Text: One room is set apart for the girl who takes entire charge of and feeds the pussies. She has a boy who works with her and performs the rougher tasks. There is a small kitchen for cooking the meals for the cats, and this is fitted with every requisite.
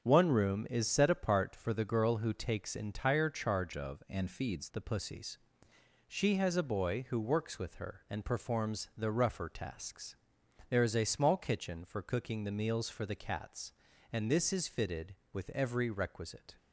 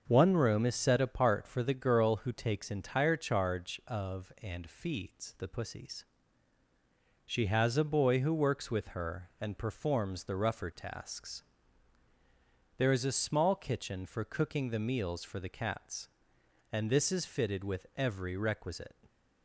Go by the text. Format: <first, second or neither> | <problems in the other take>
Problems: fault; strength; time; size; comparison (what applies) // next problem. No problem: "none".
second | starts louder than the rest; until 1.0 s; 7 dB; also in the second // changes voice from "of" to "feeds"; from 3.7 to 4.6 s; 0.9 s long